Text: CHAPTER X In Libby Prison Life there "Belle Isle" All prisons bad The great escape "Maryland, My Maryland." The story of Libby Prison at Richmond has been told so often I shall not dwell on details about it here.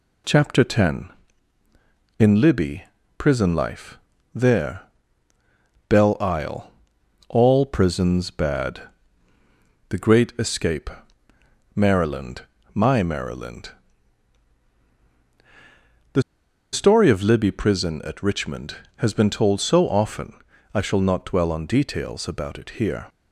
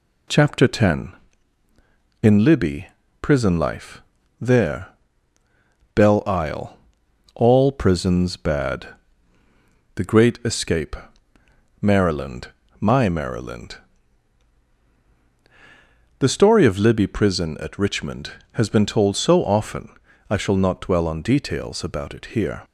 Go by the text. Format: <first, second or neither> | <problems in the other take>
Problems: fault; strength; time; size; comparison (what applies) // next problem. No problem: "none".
second | pauses between "Libby" and "Prison"; slight; at 2.8 s; 0.34 s long; slight in the second // pauses between "Life" and "there"; slight; at 3.9 s; 0.34 s long; also in the second // pauses between "there" and "Belle"; at 4.8 s; 1.0 s long; also in the second // pauses between "Isle" and "All"; noticeable; at 6.7 s; 0.56 s long; noticeable in the second // pauses between "bad" and "The"; at 8.8 s; 1.0 s long; also in the second // pauses between "escape" and "Maryland"; noticeable; at 10.8 s; 0.86 s long; noticeable in the second // pauses between "The" and "story"; noticeable; at 16.2 s; 0.51 s long // pauses between "often" and "I"; at 20.3 s; 0.40 s long; also in the second